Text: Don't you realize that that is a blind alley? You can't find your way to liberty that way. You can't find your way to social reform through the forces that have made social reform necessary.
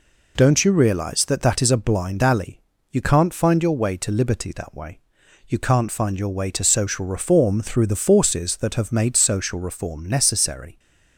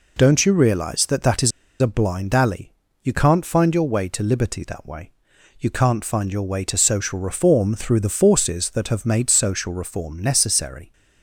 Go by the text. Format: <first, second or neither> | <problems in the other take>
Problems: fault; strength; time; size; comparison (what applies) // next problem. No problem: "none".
first | pauses between "is" and "a"; slight; at 1.5 s; 0.29 s long